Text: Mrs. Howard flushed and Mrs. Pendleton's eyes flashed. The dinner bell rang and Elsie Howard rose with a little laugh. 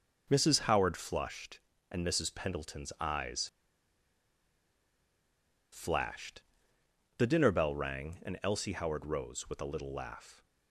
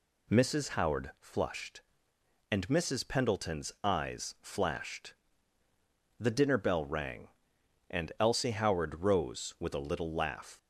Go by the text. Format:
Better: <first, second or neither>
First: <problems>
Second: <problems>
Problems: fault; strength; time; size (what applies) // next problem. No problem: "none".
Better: second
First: pauses between "eyes" and "flashed"; strong; at 3.4 s; 2.2 s long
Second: none